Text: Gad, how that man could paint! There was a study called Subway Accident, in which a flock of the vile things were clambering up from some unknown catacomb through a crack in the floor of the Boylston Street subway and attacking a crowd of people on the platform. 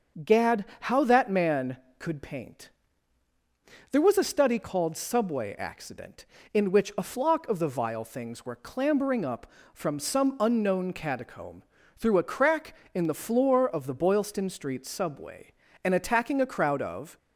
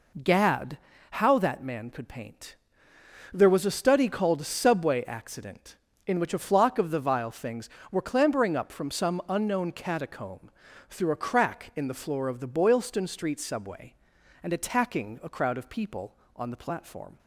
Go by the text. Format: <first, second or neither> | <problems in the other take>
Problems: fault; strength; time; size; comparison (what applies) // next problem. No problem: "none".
second | starts louder than the rest; until 1.3 s; 6.5 dB // pauses between "catacomb" and "through"; slight; at 11.6 s; 0.34 s long; also in the second // stops before "people on the platform"; at 17.1 s